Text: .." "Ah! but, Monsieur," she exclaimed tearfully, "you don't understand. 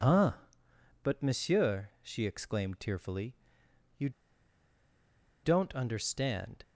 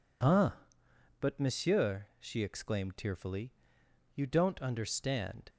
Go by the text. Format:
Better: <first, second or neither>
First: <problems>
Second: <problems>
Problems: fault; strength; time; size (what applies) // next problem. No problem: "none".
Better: second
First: pauses between "you" and "don't"; strong; at 4.0 s; 1.3 s long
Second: none